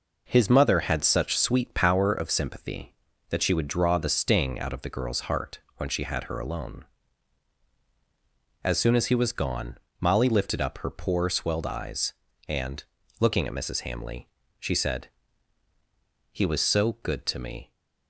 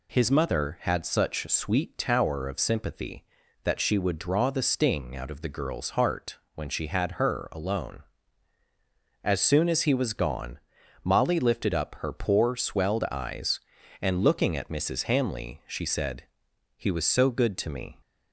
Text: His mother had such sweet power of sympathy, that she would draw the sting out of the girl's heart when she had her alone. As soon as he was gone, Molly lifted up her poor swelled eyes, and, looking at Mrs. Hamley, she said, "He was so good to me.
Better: first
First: pauses between "heart" and "when"; slight; at 5.6 s; 0.16 s long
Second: says "tower" for "power"; at 1.9 s // pauses between "heart" and "when"; slight; at 6.3 s; 0.20 s long

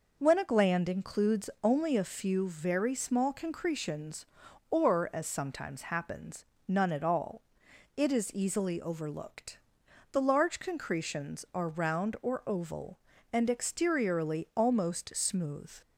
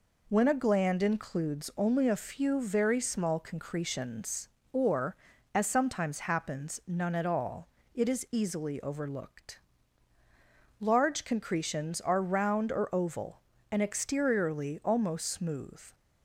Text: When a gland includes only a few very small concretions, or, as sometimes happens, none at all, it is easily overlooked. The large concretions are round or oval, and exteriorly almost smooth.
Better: first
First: none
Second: skips "The"; at 10.2 s

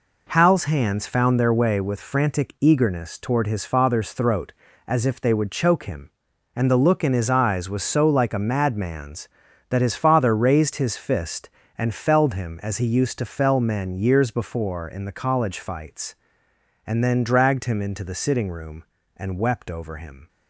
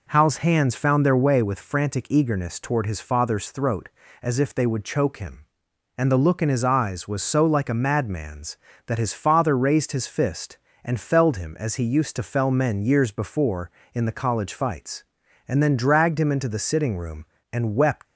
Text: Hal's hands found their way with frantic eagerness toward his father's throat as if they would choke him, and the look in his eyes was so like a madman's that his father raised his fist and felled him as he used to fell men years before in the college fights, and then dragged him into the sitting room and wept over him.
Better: first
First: none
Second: stops before "over him"; at 18.0 s

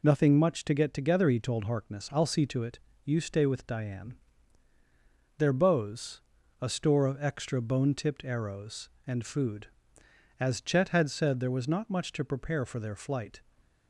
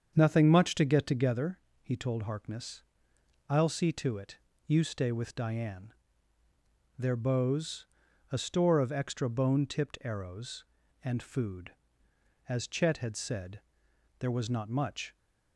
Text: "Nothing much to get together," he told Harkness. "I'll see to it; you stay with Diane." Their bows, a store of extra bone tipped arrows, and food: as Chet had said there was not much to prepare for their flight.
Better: first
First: none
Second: starts louder than the rest; strong; until 1.1 s; 7.5 dB // pauses between "said" and "there"; noticeable; at 13.6 s; 0.60 s long // stops before "to prepare for their flight"; at 15.1 s

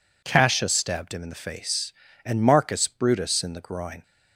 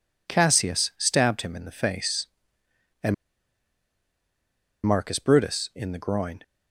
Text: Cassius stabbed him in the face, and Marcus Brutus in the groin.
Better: first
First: none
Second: pauses between "and" and "Marcus"; strong; at 3.1 s; 1.7 s long

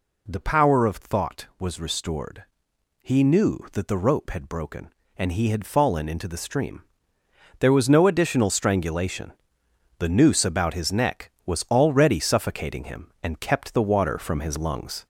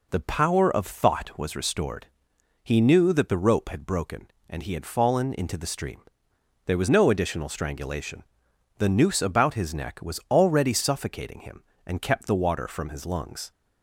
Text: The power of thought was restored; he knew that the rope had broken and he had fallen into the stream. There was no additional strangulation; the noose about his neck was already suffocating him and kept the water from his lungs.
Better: second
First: gets louder; slight; throughout; 3 dB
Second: none

